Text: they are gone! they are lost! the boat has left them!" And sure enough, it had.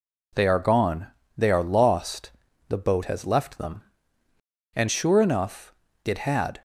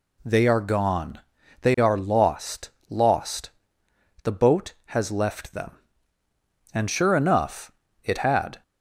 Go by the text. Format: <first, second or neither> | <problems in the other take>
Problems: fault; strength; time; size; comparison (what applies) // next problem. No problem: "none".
first | says "lost" twice; at 2.8 s